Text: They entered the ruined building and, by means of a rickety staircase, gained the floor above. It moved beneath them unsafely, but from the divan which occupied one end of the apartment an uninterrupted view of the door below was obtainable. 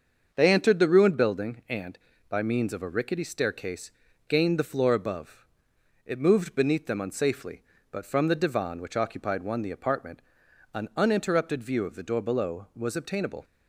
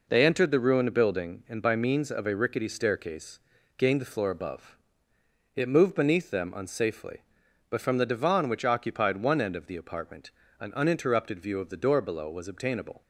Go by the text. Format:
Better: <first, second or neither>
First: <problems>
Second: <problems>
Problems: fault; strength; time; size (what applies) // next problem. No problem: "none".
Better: second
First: starts louder than the rest; until 1.3 s; 6.5 dB // skips "end of"; at 9.6 s // pauses between "apartment" and "an"; noticeable; at 10.2 s; 0.54 s long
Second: pauses between "apartment" and "an"; slight; at 10.3 s; 0.28 s long